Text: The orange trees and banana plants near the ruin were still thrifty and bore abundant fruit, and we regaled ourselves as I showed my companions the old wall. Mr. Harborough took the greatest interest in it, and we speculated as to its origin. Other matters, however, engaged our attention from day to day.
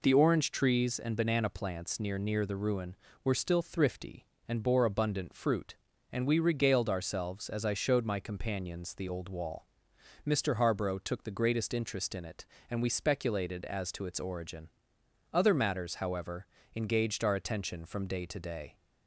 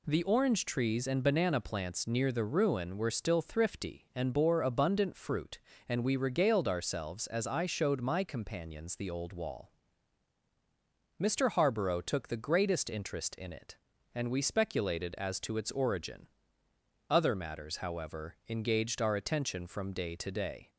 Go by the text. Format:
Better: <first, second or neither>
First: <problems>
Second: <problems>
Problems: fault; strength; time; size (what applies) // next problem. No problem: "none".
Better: second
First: says "near" twice; at 2.1 s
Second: none